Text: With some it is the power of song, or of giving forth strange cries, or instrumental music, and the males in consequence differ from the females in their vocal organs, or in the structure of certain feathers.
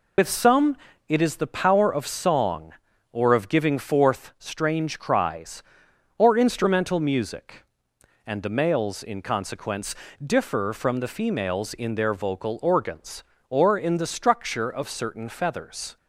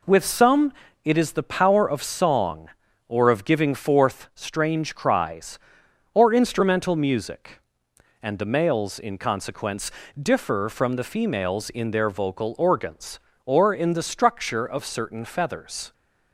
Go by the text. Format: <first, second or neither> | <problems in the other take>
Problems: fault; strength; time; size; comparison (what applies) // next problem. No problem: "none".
second | loses the start of "With"; at 0.1 s; 95 ms // pauses between "some" and "it"; slight; at 0.7 s; 0.32 s long; slight in the second // pauses between "consequence" and "differ"; slight; at 9.9 s; 0.28 s long; slight in the second